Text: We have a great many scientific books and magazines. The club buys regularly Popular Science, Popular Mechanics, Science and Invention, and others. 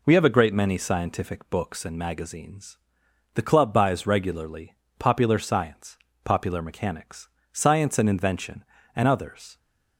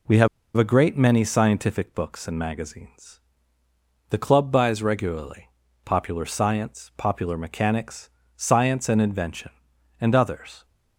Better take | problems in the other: first | pauses between "have" and "a"; slight; at 0.2 s; 0.28 s long // pauses between "regularly" and "Popular"; slight; at 5.4 s; 0.36 s long; slight in the first

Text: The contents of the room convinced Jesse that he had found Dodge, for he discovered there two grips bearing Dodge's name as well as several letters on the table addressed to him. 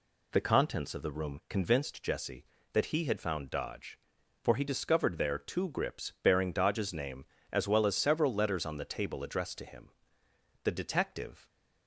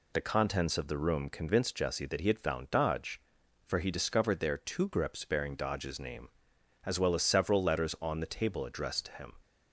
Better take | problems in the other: second | goes on to say "The detective"; noticeable; from 10.6 s on; 0.86 s long

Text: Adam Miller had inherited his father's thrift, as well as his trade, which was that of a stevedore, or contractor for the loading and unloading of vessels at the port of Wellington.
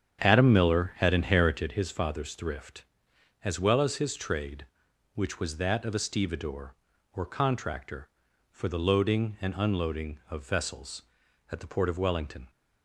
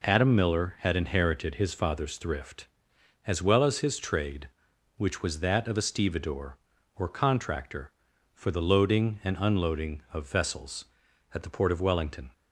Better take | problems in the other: second | starts louder than the rest; strong; until 1.8 s; 8.5 dB

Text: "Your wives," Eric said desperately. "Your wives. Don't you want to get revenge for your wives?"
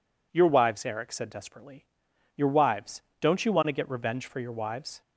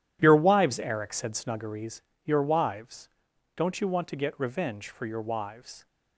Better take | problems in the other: first | says "snuggeries" for "desperately"; at 1.3 s

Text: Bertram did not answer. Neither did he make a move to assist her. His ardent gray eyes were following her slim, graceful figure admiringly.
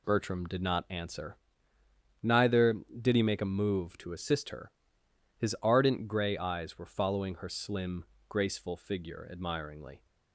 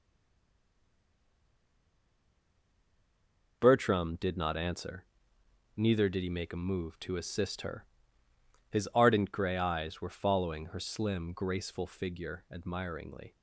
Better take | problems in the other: first | stays silent before the first word; strong; until 3.6 s; 3.6 s long

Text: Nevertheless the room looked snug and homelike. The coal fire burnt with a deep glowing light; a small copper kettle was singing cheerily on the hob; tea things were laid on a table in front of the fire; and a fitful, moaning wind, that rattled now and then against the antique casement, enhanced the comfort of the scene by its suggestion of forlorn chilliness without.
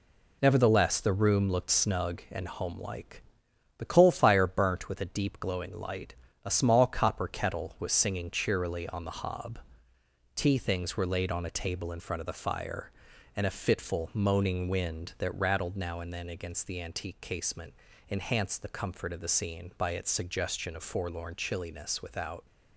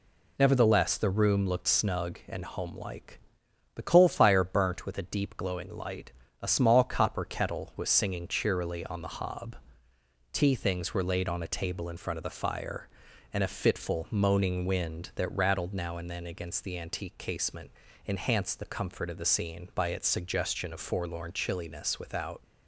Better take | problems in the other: second | gets quieter; noticeable; throughout; 6 dB

